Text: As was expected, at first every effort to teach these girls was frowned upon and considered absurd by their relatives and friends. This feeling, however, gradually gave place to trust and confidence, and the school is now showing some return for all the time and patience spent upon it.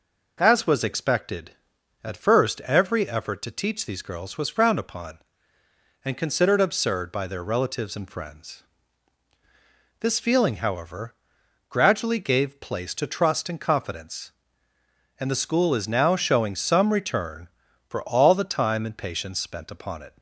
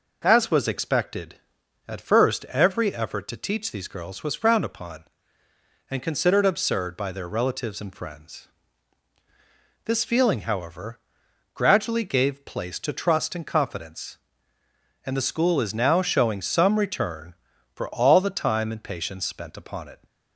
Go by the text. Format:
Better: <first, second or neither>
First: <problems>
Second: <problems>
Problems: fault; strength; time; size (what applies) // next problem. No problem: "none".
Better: neither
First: none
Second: none